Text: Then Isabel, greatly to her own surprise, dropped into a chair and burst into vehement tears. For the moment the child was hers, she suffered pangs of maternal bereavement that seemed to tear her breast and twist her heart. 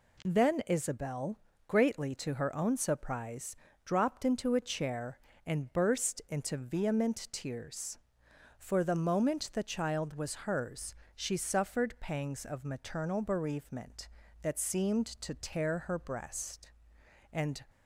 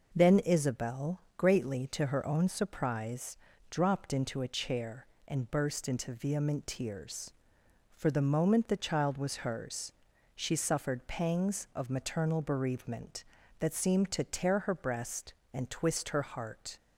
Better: second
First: stops before "twist her heart"; at 17.6 s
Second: none

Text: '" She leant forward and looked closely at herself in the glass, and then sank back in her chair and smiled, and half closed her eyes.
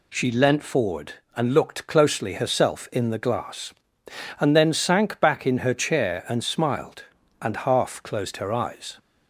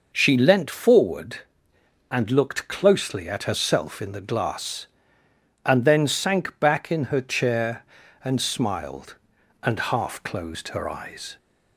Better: second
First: skips "at"; at 2.3 s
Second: none

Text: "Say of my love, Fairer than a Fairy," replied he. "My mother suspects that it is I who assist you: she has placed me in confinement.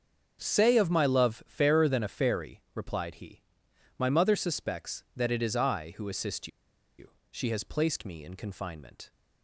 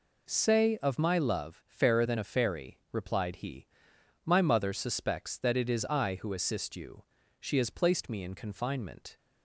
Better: second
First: starts louder than the rest; until 1.4 s; 6.5 dB // pauses between "assist" and "you"; noticeable; at 6.4 s; 0.50 s long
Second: none

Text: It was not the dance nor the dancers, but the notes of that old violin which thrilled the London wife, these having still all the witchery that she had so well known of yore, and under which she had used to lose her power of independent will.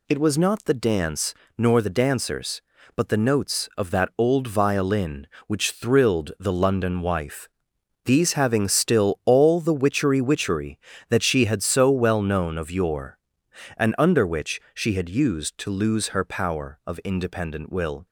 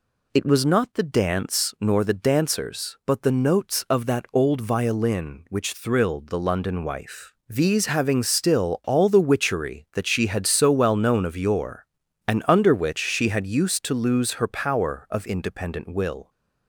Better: second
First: pauses between "dance" and "nor"; slight; at 1.3 s; 0.24 s long // says "witchery" twice; at 10.2 s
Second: none

